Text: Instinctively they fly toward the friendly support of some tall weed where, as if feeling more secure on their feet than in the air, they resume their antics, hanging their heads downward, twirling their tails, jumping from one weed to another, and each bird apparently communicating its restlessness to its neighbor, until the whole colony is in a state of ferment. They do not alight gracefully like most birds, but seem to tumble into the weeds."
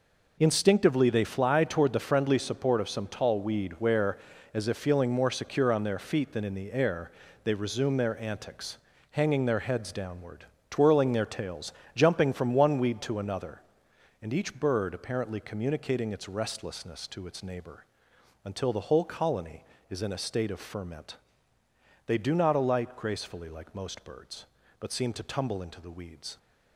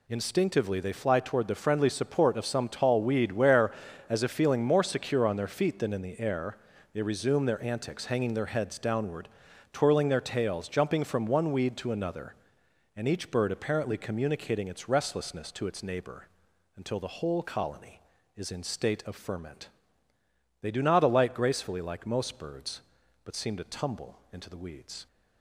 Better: first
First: none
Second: skips "a"; at 18.6 s

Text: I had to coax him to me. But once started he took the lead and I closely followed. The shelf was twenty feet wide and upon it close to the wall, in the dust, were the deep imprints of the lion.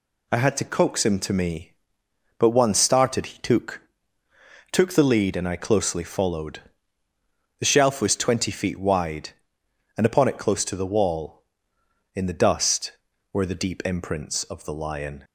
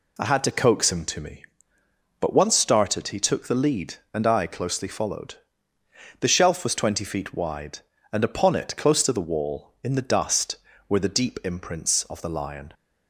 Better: second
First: says "took" twice; at 4.6 s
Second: none

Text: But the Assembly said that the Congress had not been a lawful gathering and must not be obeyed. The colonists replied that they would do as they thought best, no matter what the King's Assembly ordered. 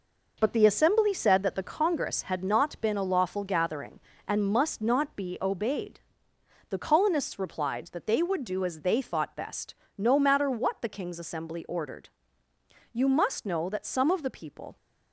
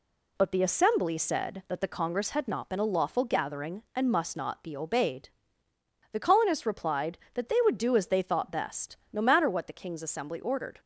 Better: second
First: goes on to say "You must know that some of the people"; strong; from 12.9 s on; 1.8 s long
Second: none

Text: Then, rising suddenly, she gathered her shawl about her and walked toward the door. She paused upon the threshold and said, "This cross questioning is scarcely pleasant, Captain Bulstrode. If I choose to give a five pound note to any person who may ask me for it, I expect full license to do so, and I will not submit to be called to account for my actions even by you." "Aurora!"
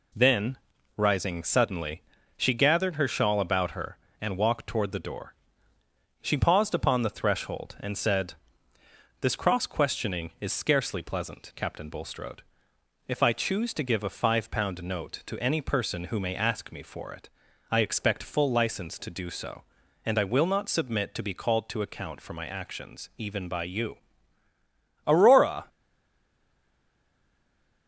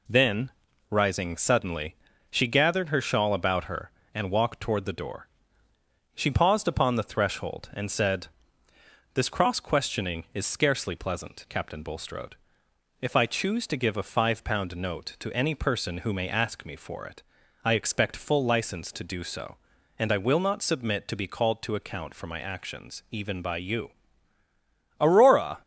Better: second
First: stays silent after the last word; from 25.6 s on; 2.2 s long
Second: none

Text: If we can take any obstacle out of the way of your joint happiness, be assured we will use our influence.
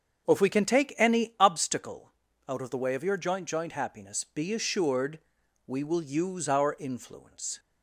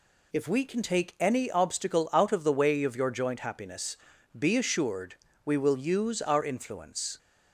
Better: second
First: starts louder than the rest; until 1.2 s; 6.5 dB // pauses between "obstacle" and "out"; at 2.1 s; 0.38 s long // says "joint" twice; at 3.4 s // pauses between "assured" and "we"; noticeable; at 5.1 s; 0.48 s long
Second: pauses between "assured" and "we"; slight; at 5.1 s; 0.28 s long

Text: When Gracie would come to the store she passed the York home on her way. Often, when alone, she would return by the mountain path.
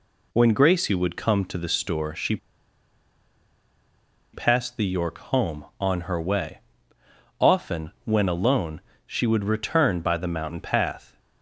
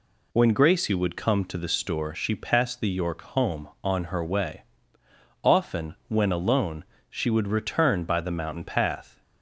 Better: second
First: pauses between "she" and "passed"; strong; at 2.3 s; 1.9 s long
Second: none

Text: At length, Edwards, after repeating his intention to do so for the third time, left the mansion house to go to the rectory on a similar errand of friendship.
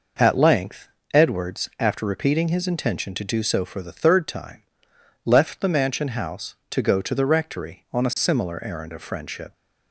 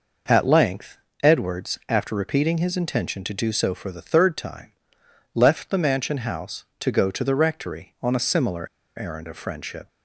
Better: first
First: none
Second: pauses between "similar" and "errand"; slight; at 8.6 s; 0.29 s long

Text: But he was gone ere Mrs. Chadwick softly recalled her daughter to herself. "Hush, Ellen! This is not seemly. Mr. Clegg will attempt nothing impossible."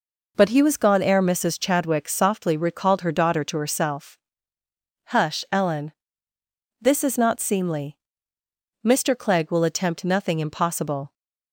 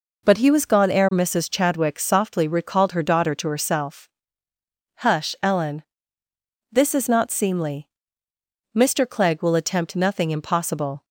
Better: neither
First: none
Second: none

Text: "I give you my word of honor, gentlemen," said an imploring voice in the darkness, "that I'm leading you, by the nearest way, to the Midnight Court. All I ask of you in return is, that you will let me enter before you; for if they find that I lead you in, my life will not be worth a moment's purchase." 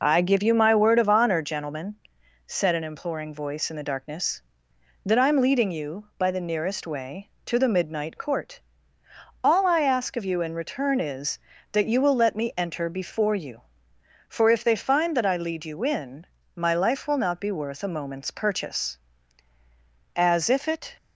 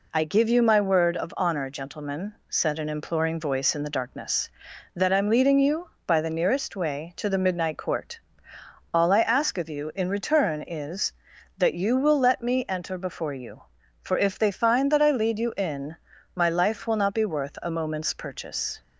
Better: second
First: goes on to say "As if it"; noticeable; from 20.1 s on; 0.80 s long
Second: none

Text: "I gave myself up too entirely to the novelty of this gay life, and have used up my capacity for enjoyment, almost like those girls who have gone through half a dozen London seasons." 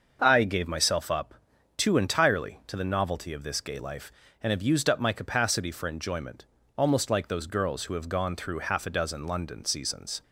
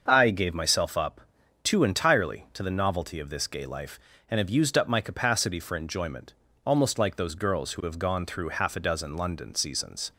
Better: neither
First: starts louder than the rest; until 1.2 s; 6.5 dB // pauses between "up" and "too"; noticeable; at 1.3 s; 0.46 s long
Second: starts louder than the rest; until 1.0 s; 6.5 dB // pauses between "up" and "too"; noticeable; at 1.1 s; 0.46 s long

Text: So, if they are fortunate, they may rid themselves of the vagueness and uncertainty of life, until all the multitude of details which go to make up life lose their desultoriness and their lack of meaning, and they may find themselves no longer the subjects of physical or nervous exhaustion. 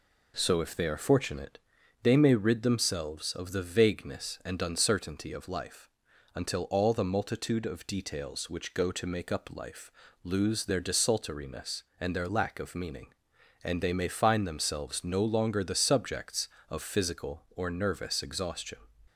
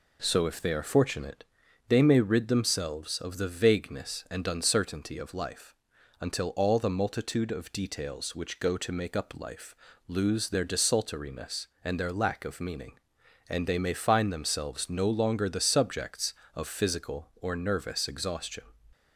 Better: neither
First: pauses between "life" and "lose"; slight; at 9.9 s; 0.34 s long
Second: pauses between "life" and "lose"; slight; at 9.7 s; 0.34 s long

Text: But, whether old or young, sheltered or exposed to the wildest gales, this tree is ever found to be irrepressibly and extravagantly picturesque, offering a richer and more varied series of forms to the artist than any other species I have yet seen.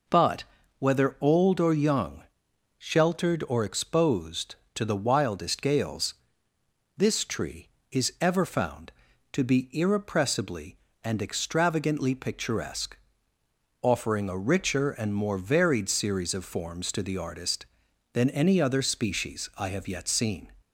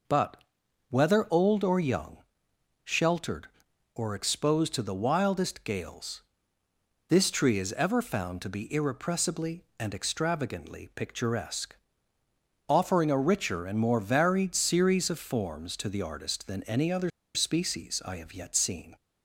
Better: first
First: none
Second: pauses between "other" and "species"; slight; at 17.0 s; 0.25 s long

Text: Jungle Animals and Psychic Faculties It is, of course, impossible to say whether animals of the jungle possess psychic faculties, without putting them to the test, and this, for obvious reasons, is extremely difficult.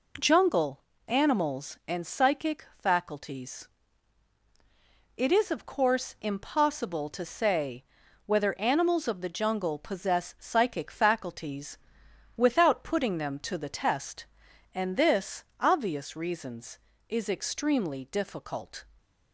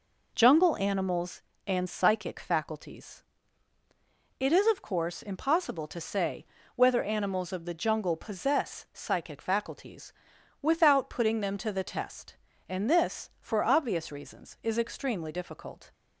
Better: second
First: pauses between "Jungle" and "Animals"; slight; at 0.8 s; 0.26 s long // pauses between "Faculties" and "It"; strong; at 3.6 s; 1.5 s long // pauses between "say" and "whether"; at 7.8 s; 0.40 s long // skips "for"; at 15.5 s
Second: pauses between "Faculties" and "It"; at 3.2 s; 1.1 s long // pauses between "say" and "whether"; slight; at 6.4 s; 0.30 s long

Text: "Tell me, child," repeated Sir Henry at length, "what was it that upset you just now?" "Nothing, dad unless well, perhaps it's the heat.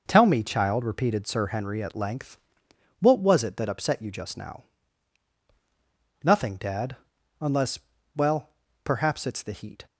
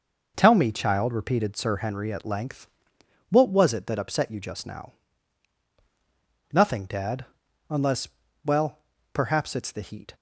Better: neither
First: pauses between "dad" and "unless"; noticeable; at 6.9 s; 0.46 s long // pauses between "unless" and "well"; at 7.7 s; 0.38 s long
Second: pauses between "dad" and "unless"; noticeable; at 7.2 s; 0.46 s long // pauses between "unless" and "well"; at 8.0 s; 0.38 s long

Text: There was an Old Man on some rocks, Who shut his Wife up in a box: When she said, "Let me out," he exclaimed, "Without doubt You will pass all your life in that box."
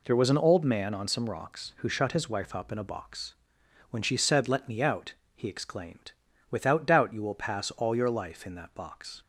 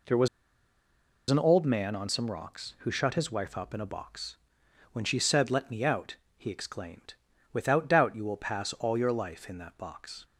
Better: first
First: none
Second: pauses between "was" and "an"; at 0.2 s; 1.0 s long

